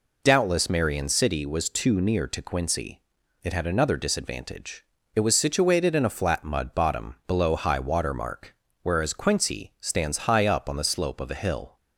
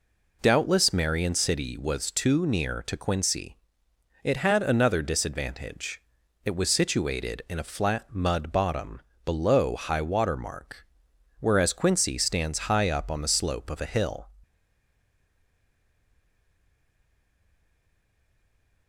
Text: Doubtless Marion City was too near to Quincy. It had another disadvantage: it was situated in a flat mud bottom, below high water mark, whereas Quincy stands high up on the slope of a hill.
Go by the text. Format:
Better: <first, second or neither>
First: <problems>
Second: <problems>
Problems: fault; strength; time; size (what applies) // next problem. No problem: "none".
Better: first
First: none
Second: stays silent after the last word; strong; from 14.4 s on; 4.4 s long